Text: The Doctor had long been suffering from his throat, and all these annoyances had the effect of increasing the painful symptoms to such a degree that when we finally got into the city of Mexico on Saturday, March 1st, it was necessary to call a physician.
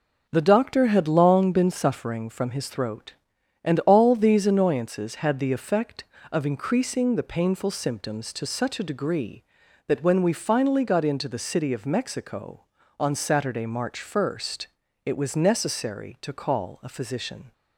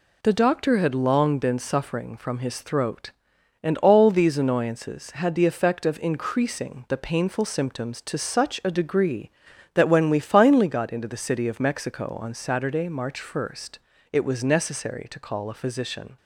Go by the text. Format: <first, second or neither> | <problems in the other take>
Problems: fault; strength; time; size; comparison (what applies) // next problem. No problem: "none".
neither | none